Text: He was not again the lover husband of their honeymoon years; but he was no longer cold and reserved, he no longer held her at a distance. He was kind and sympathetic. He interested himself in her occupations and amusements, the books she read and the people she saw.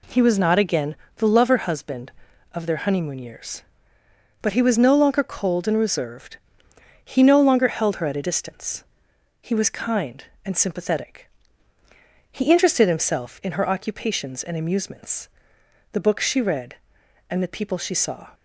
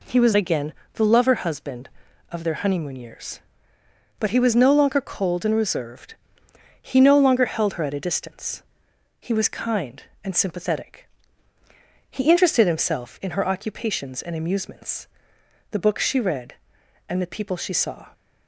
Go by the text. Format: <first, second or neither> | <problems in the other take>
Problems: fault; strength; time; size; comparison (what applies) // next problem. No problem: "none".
first | skips "not"; at 0.3 s // pauses between "again" and "the"; slight; at 0.7 s; 0.20 s long; slight in the first